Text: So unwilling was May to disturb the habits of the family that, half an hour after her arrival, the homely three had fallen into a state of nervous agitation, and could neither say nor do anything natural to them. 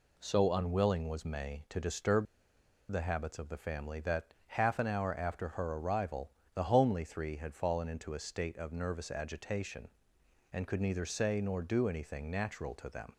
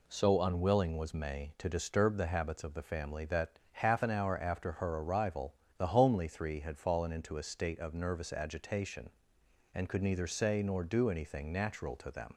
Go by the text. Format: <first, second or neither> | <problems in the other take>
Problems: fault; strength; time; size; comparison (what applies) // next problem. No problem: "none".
second | pauses between "disturb" and "the"; noticeable; at 2.2 s; 0.65 s long